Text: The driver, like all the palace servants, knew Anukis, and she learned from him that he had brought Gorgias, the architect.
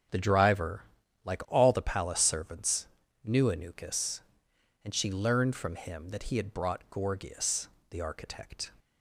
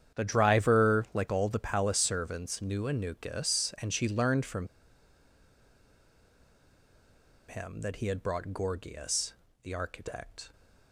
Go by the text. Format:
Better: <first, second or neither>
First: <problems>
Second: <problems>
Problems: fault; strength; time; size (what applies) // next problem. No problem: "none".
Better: first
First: starts louder than the rest; strong; until 1.6 s; 8 dB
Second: starts louder than the rest; strong; until 1.2 s; 9 dB // pauses between "from" and "him"; strong; at 4.6 s; 2.8 s long